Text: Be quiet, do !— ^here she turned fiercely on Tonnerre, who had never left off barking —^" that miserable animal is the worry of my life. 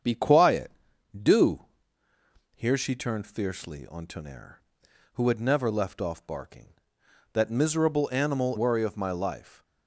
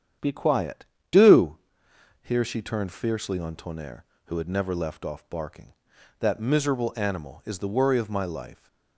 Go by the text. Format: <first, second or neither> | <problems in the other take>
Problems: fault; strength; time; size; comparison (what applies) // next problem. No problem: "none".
second | starts louder than the rest; strong; until 1.5 s; 7.5 dB; strong in the second // skips "is the"; at 8.5 s